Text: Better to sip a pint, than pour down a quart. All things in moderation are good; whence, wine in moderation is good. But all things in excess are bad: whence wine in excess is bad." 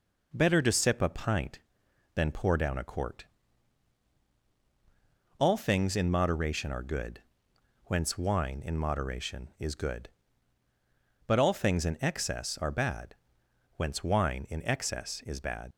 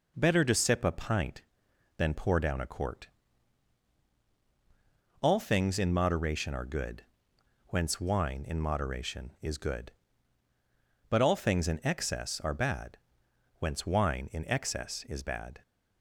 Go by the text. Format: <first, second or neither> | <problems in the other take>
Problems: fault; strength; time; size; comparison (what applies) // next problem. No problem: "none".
second | leaves "bad" unfinished; at 15.7 s; 85 ms